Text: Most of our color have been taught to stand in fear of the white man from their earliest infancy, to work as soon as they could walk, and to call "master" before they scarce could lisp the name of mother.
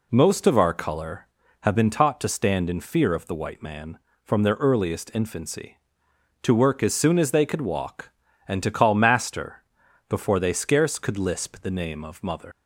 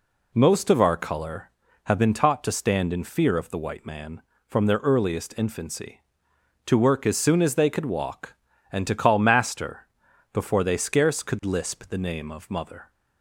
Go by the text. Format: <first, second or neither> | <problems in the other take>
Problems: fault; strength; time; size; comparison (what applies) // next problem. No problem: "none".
second | pauses between "master" and "before"; at 9.6 s; 0.44 s long; also in the second // leaves "mother" unfinished; at 12.5 s; 105 ms